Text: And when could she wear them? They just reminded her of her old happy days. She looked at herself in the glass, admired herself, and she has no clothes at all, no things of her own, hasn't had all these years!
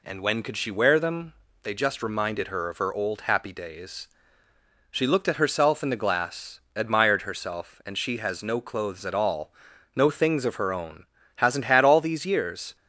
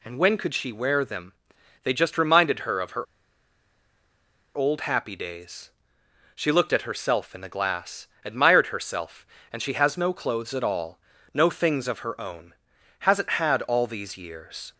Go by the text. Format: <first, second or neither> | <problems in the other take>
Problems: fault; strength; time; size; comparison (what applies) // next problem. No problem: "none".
first | pauses between "her" and "old"; strong; at 3.0 s; 1.5 s long